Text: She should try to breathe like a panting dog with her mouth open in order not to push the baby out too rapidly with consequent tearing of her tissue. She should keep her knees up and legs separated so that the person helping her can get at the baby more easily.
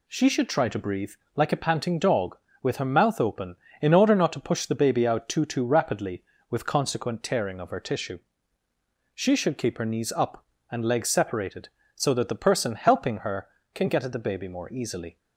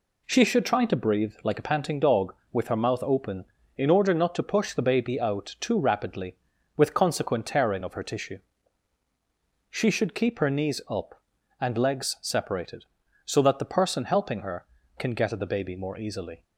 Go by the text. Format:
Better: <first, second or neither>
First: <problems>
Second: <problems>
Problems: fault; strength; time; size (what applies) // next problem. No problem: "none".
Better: second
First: pauses between "breathe" and "like"; slight; at 1.1 s; 0.22 s long // says "too" twice; at 5.4 s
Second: none